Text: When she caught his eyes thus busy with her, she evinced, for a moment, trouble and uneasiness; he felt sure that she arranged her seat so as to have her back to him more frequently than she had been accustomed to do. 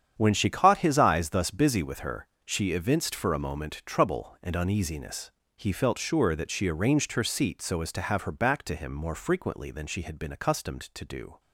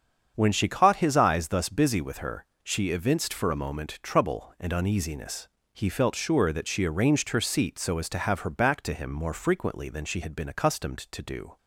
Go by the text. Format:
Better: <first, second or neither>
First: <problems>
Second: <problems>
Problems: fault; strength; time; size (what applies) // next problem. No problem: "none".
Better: second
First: gets quieter; strong; throughout; 12.5 dB // starts louder than the rest; strong; until 1.1 s; 8.5 dB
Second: starts louder than the rest; strong; until 1.3 s; 7.5 dB